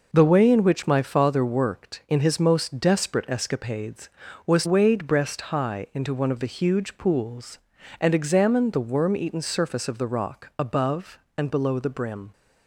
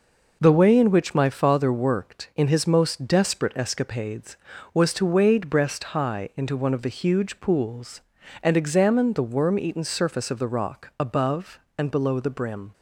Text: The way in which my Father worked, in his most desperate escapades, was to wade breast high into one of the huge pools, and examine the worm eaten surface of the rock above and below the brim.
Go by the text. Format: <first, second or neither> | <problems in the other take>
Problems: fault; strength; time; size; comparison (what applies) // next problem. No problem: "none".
second | skips "to"; at 4.6 s